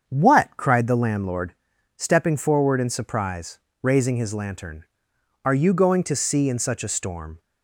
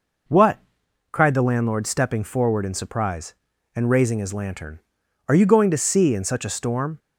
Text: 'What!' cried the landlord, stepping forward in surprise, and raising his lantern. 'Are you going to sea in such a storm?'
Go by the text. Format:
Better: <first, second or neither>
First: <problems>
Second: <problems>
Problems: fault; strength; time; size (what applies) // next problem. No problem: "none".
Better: second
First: starts louder than the rest; strong; until 1.0 s; 7 dB // skips "and"; at 3.6 s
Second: none